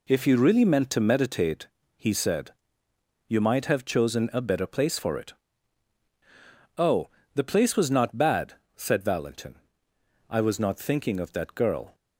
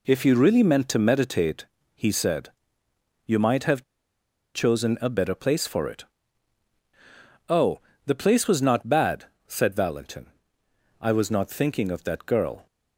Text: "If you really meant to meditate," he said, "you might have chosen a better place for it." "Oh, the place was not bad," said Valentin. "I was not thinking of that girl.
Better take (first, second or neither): first